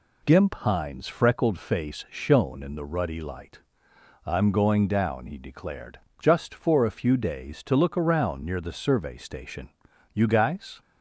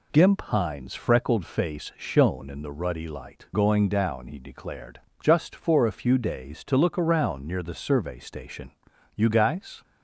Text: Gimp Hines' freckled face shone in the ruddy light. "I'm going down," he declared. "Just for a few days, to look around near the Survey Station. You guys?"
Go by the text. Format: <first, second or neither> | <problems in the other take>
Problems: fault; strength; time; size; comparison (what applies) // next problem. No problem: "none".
first | skips "I'm"; at 3.5 s